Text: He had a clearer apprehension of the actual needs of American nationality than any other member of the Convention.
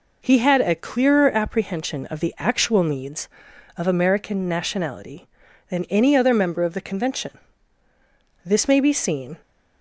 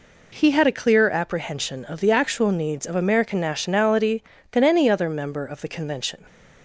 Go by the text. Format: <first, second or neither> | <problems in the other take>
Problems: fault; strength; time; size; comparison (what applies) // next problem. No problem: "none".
second | goes on to say "This may be seen"; noticeable; from 8.4 s on; 0.92 s long